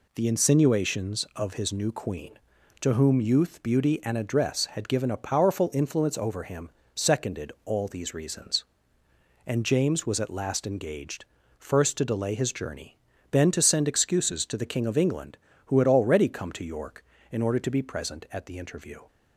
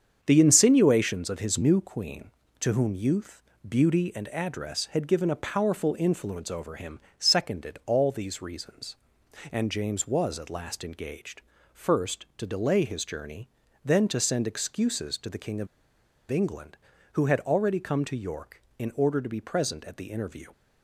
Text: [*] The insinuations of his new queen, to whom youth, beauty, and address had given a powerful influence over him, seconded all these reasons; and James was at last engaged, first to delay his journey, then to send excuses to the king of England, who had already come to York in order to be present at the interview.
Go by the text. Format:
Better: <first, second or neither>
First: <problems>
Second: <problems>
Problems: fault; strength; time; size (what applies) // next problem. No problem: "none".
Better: first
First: none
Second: starts louder than the rest; strong; until 1.2 s; 7.5 dB // pauses between "of" and "England"; noticeable; at 15.6 s; 0.62 s long